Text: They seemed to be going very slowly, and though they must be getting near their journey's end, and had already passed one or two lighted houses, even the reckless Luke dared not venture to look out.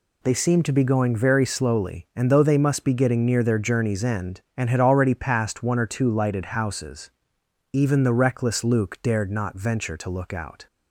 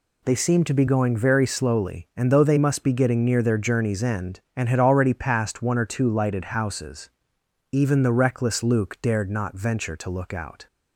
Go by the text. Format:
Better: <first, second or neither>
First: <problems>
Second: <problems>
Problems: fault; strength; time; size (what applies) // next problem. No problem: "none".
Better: neither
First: none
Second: none